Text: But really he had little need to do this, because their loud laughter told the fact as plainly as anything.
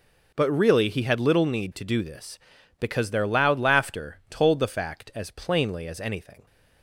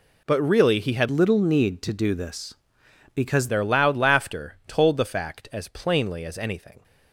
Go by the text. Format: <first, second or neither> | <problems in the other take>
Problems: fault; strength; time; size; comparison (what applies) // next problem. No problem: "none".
first | changes voice from "little" to "because"; from 1.0 to 3.4 s; 2.4 s long